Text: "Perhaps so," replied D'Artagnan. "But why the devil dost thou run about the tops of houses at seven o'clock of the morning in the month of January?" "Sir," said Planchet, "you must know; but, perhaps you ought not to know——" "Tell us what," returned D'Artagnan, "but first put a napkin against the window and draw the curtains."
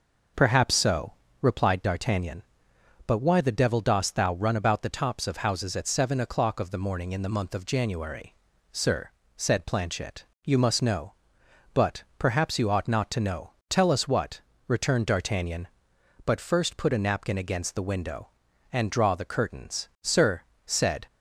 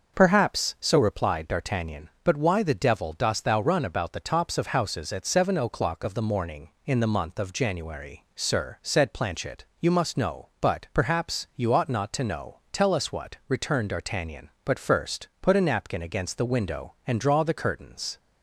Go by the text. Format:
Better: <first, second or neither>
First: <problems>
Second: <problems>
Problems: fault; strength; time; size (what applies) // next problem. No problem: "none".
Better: second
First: starts louder than the rest; noticeable; until 1.6 s; 6 dB // goes on to say "Sir said"; noticeable; from 20.0 s on; 1.0 s long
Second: starts louder than the rest; until 1.1 s; 6.5 dB